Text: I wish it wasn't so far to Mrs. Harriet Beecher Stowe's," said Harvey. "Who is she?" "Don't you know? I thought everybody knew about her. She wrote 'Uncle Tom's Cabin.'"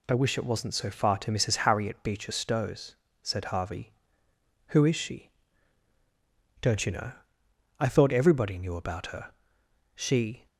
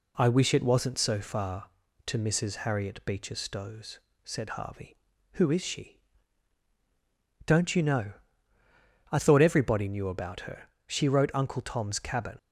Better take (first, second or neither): second